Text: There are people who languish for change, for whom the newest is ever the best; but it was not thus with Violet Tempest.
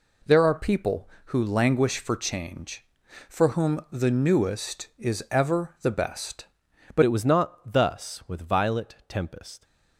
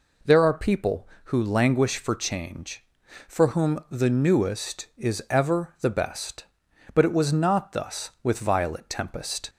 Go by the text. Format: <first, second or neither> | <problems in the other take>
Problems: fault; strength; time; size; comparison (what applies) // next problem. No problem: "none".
second | changes voice at "it"; from 7.0 s on; 2.6 s long